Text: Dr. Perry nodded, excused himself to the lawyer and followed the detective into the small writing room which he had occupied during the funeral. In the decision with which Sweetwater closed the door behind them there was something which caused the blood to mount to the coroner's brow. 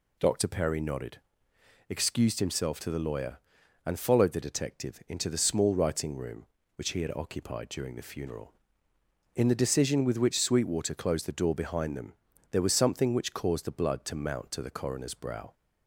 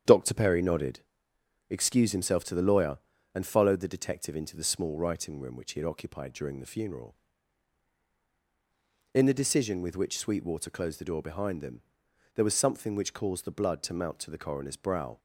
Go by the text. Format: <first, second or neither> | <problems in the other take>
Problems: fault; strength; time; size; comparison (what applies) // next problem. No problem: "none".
first | starts louder than the rest; strong; until 1.0 s; 8.5 dB // pauses between "them" and "there"; noticeable; at 11.8 s; 0.54 s long; also in the first